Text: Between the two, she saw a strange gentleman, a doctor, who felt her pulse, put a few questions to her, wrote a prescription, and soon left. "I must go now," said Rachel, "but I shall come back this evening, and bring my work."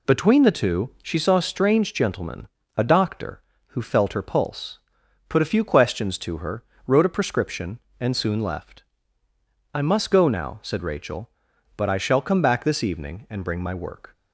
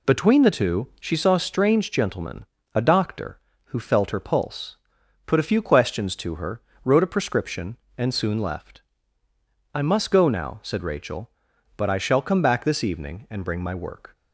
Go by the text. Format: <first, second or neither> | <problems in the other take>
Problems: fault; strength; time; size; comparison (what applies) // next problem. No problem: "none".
neither | none